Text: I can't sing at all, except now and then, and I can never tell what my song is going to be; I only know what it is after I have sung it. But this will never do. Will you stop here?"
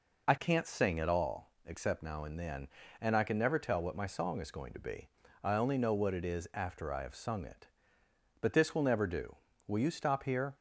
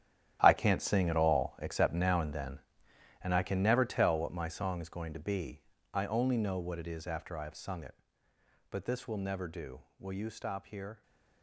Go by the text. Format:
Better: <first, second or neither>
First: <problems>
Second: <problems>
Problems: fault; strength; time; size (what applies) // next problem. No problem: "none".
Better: first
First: none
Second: gets quieter; strong; throughout; 13.5 dB